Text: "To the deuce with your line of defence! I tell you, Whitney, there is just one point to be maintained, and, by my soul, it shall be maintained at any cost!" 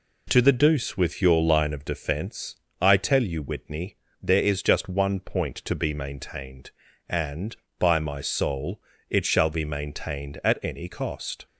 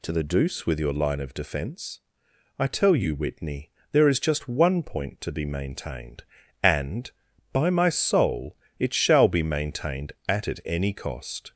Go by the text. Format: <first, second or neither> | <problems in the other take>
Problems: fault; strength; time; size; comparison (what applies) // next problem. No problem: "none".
first | says "at" twice; at 10.4 s